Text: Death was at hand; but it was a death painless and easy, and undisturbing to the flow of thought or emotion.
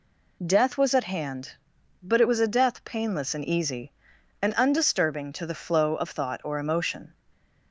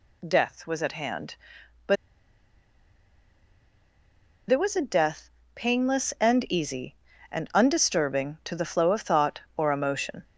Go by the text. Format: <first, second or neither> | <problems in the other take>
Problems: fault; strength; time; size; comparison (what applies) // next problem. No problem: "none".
first | pauses between "but" and "it"; strong; at 1.9 s; 2.5 s long // pauses between "death" and "painless"; slight; at 5.2 s; 0.26 s long